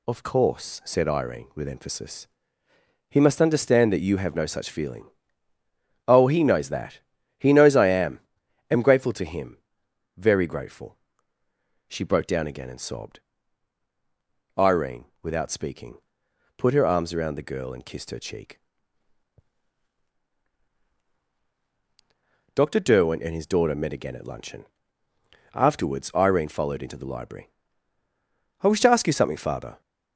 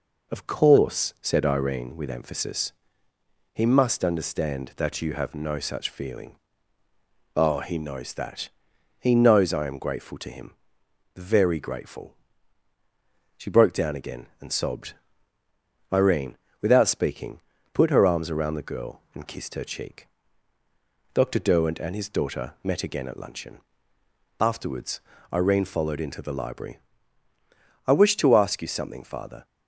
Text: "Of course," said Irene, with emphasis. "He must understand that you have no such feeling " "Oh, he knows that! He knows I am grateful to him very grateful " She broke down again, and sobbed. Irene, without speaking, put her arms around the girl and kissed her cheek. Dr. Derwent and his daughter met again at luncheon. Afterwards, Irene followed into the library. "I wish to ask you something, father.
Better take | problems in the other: second | says "am" twice; at 8.7 s // pauses between "him" and "very"; noticeable; at 9.5 s; 0.58 s long; noticeable in the second

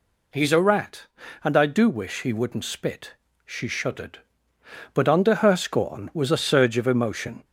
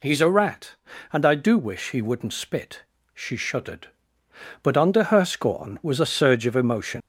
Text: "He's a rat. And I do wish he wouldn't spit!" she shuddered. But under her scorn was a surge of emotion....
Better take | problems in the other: first | leaves "emotion" unfinished; at 7.0 s; 130 ms

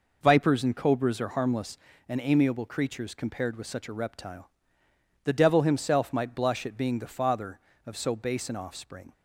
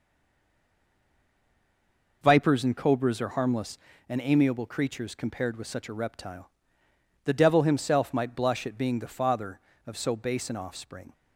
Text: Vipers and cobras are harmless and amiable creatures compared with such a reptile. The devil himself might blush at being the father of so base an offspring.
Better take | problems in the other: first | stays silent before the first word; until 2.2 s; 2.2 s long

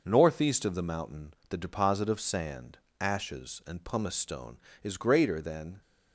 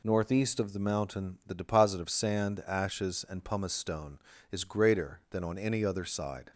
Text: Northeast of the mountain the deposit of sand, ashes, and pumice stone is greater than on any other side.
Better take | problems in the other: second | pauses between "mountain" and "the"; slight; at 1.3 s; 0.16 s long // stops before "on any other side"; at 5.8 s

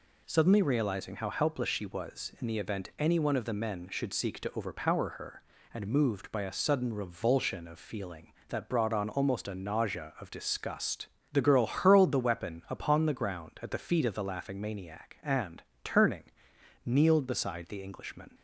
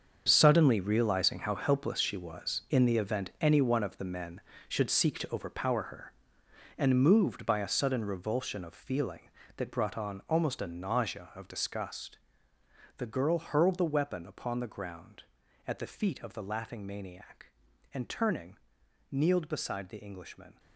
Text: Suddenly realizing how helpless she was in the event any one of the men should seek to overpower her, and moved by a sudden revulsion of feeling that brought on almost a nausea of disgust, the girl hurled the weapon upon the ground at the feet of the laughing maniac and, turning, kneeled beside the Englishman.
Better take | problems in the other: first | gets quieter; strong; throughout; 12.5 dB

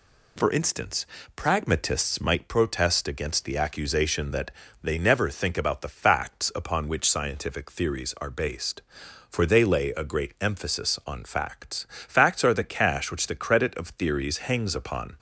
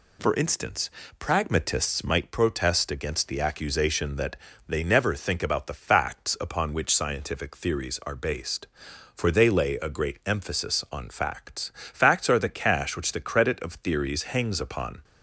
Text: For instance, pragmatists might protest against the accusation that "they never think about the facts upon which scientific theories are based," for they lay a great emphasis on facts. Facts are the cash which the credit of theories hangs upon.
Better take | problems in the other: neither | pauses between "that" and "they"; slight; the same in both

